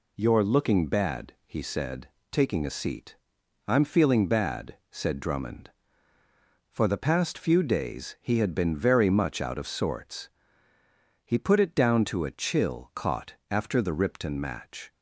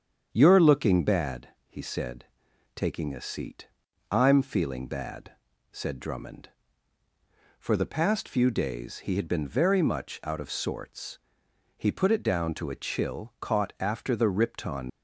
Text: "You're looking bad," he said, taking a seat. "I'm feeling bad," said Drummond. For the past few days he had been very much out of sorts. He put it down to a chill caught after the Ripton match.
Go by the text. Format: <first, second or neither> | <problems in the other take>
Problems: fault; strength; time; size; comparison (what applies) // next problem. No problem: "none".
first | starts louder than the rest; strong; until 1.3 s; 8 dB // stops before "match"; at 14.8 s